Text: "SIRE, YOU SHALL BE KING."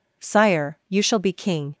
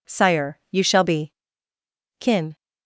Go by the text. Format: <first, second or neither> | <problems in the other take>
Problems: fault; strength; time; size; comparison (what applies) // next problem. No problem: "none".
first | says "Kin" for "KING"; at 2.1 s